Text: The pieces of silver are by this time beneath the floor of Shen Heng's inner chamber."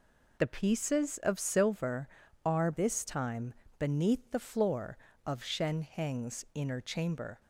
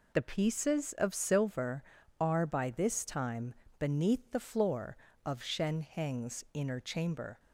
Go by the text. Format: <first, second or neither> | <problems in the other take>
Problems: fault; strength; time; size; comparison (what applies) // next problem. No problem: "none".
second | skips "by"; at 2.7 s // pauses between "time" and "beneath"; slight; at 3.5 s; 0.24 s long; slight in the second